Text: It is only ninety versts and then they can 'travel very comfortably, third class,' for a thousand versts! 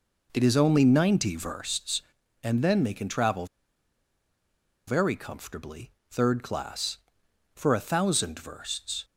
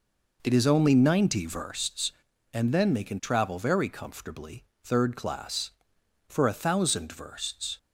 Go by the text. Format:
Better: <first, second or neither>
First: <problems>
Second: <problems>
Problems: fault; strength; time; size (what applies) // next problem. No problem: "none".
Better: second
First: pauses between "travel" and "very"; strong; at 3.4 s; 1.4 s long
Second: none